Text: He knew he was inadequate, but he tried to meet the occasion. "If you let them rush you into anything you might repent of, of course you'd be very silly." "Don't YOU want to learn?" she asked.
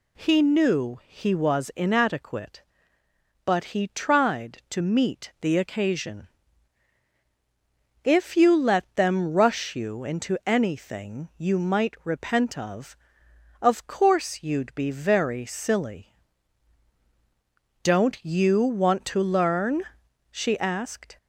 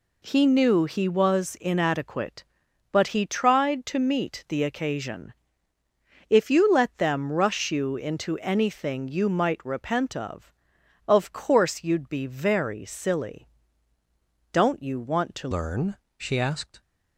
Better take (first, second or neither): first